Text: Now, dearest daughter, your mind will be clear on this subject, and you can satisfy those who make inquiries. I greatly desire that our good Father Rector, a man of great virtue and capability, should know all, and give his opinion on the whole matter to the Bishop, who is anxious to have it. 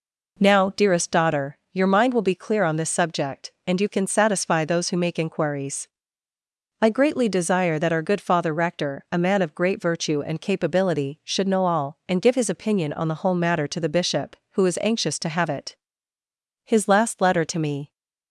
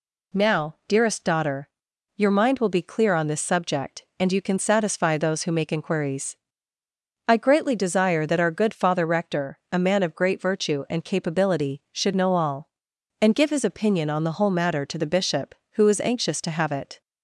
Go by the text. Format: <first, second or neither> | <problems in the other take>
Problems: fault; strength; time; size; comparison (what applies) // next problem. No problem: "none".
second | goes on to say "His last letter to me"; noticeable; from 16.6 s on; 1.2 s long